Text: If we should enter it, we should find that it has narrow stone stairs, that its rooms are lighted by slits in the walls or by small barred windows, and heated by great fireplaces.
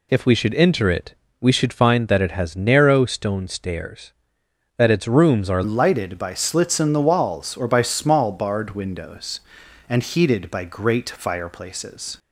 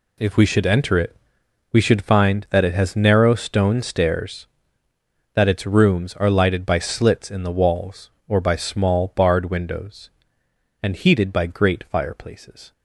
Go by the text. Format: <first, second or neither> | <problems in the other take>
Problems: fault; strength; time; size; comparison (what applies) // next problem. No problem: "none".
second | changes voice at "lighted"; from 5.6 s on; 6.5 s long